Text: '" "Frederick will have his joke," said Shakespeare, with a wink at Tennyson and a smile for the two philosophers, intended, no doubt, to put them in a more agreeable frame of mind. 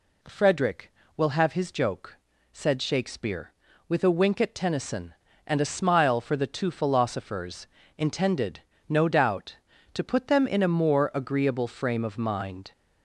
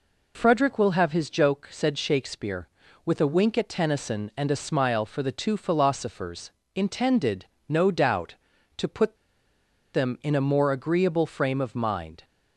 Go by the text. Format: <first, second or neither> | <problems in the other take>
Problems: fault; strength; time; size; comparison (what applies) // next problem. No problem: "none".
first | pauses between "put" and "them"; noticeable; at 9.1 s; 0.77 s long